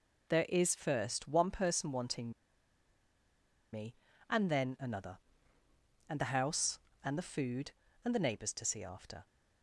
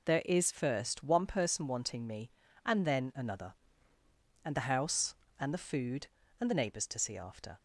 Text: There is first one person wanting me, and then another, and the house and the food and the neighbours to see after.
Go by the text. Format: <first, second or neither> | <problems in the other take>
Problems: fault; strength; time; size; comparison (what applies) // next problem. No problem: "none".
second | pauses between "wanting" and "me"; strong; at 2.3 s; 1.4 s long